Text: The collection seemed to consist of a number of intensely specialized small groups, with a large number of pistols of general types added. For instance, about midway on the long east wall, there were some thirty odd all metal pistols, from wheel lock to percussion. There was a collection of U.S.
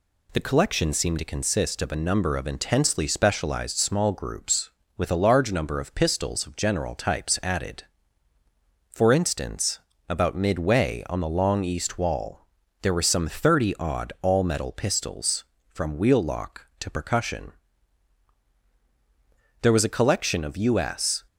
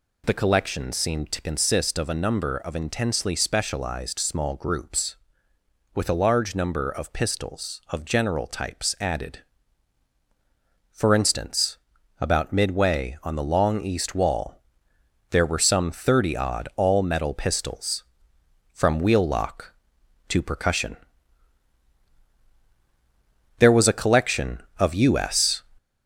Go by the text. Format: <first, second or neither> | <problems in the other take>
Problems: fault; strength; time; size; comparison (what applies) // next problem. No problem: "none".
first | gets louder; throughout; 3.5 dB